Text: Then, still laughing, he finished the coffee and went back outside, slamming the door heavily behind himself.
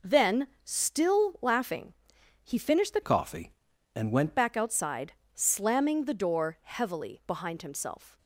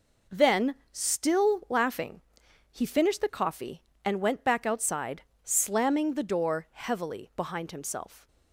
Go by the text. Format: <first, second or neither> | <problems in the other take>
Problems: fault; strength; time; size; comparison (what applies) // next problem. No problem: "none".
second | changes voice from "coffee" to "went"; from 3.0 to 4.3 s; 1.3 s long